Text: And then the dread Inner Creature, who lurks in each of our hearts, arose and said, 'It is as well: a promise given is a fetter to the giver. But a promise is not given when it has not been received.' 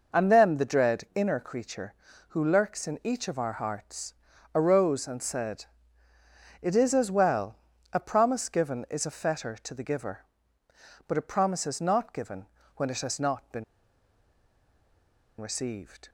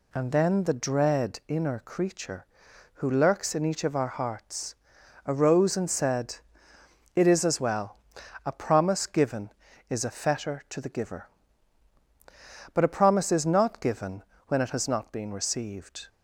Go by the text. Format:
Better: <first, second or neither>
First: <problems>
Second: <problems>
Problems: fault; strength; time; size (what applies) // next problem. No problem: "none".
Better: second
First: pauses between "given" and "when"; slight; at 12.4 s; 0.30 s long // pauses between "been" and "received"; strong; at 13.6 s; 1.7 s long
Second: pauses between "given" and "when"; slight; at 14.2 s; 0.24 s long